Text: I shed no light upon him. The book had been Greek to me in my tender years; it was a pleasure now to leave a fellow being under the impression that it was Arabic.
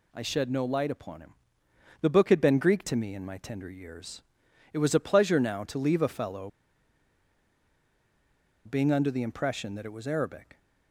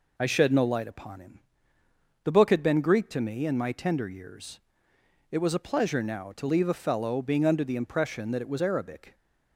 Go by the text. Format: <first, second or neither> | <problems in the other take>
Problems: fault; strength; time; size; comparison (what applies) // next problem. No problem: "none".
second | pauses between "fellow" and "being"; strong; at 6.4 s; 2.1 s long